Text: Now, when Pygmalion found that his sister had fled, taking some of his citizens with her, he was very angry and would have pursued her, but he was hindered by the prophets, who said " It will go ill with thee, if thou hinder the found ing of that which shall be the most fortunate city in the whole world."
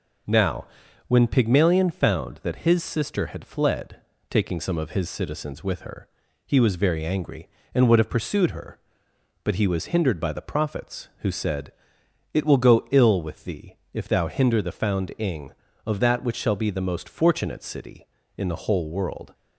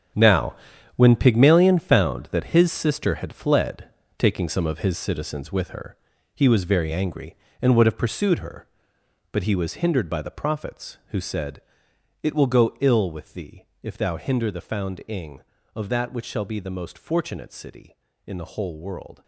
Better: first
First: none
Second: gets quieter; strong; throughout; 12 dB

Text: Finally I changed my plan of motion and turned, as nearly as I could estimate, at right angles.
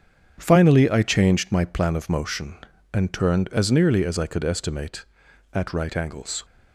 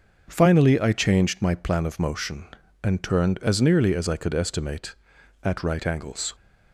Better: second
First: gets quieter; strong; throughout; 8.5 dB // starts louder than the rest; strong; until 1.3 s; 8 dB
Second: starts louder than the rest; until 1.2 s; 6.5 dB

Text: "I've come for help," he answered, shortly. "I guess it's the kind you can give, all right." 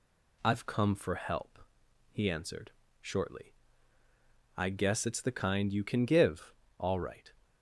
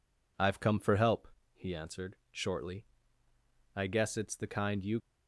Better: first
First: none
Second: stops before "can give all right"; at 5.0 s

